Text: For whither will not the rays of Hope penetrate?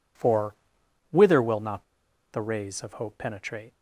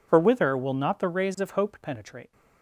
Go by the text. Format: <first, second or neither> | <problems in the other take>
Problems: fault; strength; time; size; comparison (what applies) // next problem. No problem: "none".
second | pauses between "For" and "whither"; noticeable; at 0.5 s; 0.56 s long // pauses between "not" and "the"; noticeable; at 1.8 s; 0.48 s long